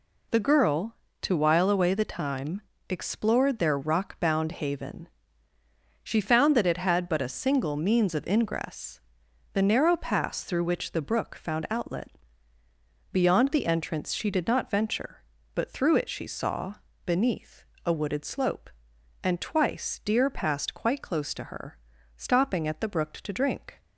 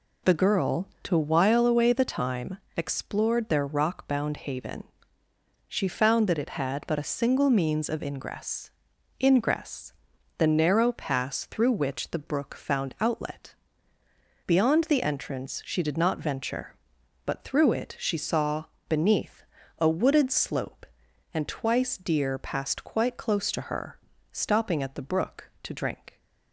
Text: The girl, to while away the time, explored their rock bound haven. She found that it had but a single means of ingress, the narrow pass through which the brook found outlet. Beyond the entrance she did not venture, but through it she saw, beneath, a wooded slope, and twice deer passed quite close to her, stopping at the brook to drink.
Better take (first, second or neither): first